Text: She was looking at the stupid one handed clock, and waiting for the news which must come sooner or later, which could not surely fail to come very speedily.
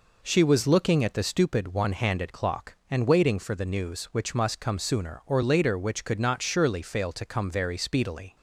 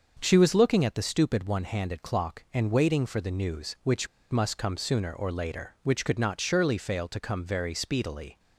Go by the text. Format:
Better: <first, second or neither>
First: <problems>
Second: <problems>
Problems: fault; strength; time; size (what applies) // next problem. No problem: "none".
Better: first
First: none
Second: starts louder than the rest; until 1.2 s; 6.5 dB // pauses between "which" and "must"; slight; at 4.0 s; 0.25 s long